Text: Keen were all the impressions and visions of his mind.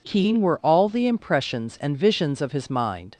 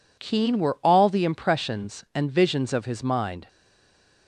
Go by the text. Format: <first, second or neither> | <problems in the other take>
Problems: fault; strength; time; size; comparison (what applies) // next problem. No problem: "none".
first | stays silent after the last word; slight; from 3.4 s on; 0.8 s long